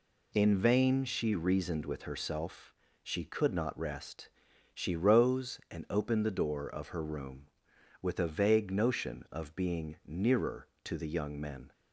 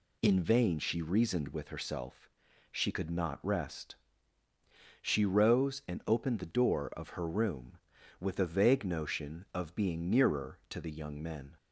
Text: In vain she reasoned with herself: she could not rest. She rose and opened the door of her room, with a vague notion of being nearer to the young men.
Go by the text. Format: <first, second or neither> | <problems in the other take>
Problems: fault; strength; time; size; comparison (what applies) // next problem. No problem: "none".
neither | none